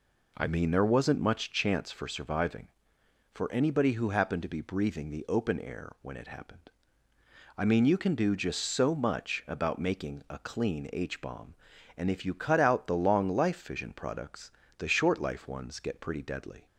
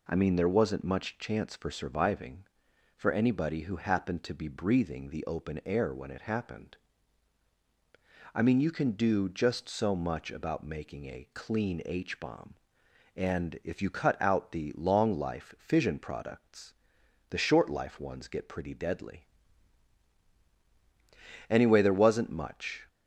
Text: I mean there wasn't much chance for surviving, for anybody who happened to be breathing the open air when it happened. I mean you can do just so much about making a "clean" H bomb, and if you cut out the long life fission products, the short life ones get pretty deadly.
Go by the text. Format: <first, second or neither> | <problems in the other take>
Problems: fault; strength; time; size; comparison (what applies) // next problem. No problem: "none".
first | goes on to say "Anyway there wasn't much"; from 21.4 s on; 1.3 s long